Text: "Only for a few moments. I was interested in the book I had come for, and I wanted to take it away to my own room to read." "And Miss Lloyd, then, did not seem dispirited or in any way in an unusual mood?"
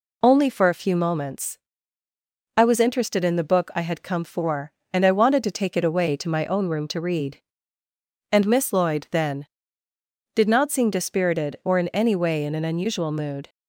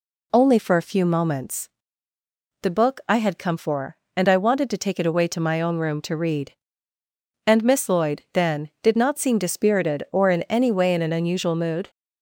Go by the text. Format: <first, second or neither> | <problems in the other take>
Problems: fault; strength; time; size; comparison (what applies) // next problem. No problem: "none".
first | skips "I was interested in"; at 2.1 s